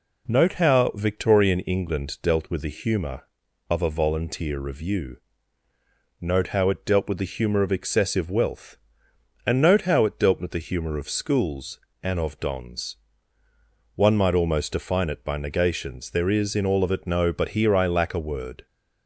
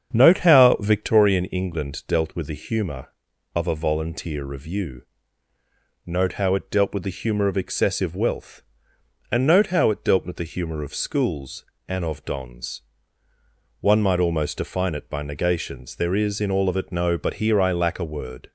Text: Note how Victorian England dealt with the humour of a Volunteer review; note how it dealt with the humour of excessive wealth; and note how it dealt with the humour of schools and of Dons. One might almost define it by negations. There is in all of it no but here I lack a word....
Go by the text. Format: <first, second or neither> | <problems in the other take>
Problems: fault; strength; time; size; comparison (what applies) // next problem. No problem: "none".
first | starts louder than the rest; strong; until 1.2 s; 8 dB